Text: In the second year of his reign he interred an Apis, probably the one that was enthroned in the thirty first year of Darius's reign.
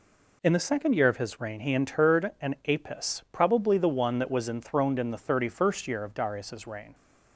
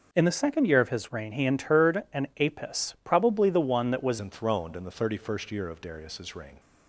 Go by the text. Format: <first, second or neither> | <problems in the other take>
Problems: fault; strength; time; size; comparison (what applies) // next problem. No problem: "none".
first | changes voice at "enthroned"; from 4.1 s on; 2.4 s long